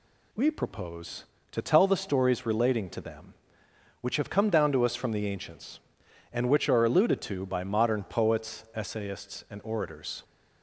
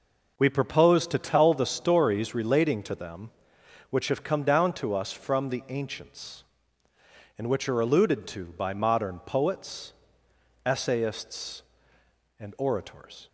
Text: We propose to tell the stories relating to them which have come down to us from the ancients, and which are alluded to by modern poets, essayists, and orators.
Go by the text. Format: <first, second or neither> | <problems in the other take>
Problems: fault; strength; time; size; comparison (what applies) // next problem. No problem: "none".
neither | none